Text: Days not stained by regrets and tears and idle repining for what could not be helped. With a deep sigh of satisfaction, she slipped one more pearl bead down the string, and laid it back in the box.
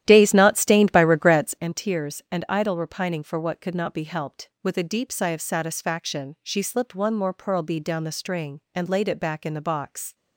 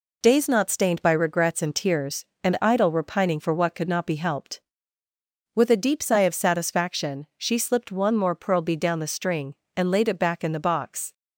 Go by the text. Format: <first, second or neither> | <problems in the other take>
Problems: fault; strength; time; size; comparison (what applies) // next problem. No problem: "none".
second | starts louder than the rest; strong; until 1.7 s; 12 dB